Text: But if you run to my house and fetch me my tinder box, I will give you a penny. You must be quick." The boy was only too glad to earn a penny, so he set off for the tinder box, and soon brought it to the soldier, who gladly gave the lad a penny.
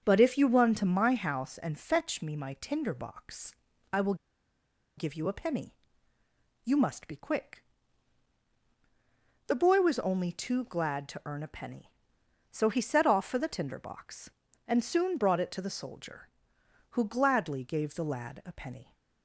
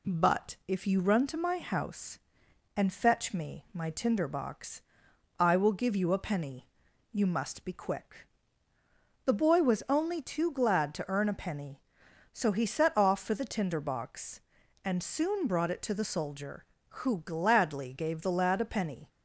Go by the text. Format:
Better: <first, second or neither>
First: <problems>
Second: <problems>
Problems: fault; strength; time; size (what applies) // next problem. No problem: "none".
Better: second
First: starts louder than the rest; until 1.0 s; 7 dB // pauses between "will" and "give"; noticeable; at 4.1 s; 0.83 s long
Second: none